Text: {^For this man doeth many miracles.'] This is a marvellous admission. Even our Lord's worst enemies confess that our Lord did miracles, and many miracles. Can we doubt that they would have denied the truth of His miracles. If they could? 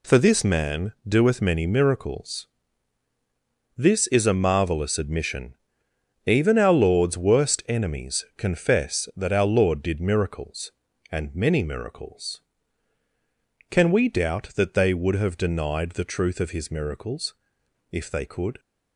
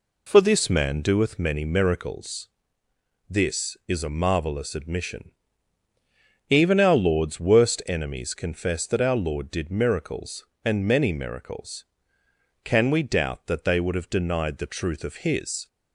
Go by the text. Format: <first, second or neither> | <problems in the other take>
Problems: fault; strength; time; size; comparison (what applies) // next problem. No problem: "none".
first | stops before "miracles If they could"; at 15.6 s